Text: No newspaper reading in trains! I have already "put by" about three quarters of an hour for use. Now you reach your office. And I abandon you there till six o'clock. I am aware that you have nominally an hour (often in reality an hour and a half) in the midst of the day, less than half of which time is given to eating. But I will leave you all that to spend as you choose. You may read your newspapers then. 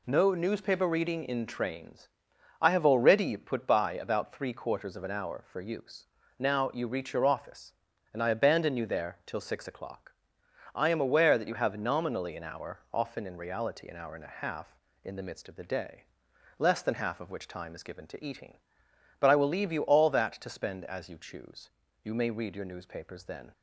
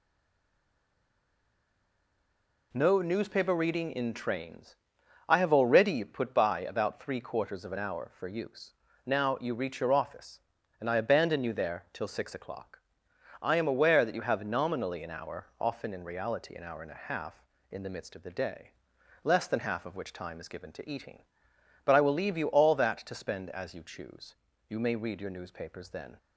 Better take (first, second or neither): first